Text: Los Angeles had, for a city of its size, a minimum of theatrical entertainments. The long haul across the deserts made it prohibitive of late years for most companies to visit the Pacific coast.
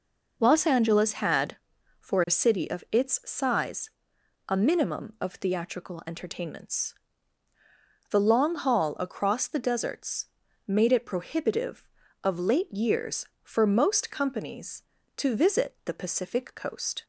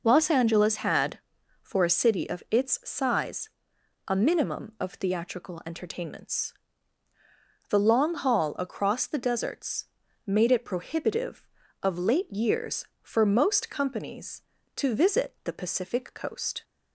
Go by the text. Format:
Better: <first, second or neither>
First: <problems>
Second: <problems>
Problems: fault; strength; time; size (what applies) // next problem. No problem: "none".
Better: neither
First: pauses between "deserts" and "made"; at 10.2 s; 0.40 s long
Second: pauses between "deserts" and "made"; at 9.8 s; 0.40 s long